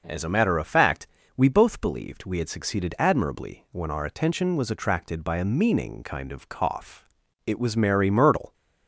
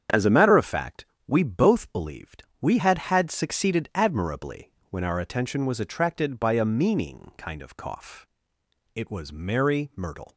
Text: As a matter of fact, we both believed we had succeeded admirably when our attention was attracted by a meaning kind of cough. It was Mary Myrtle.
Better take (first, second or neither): first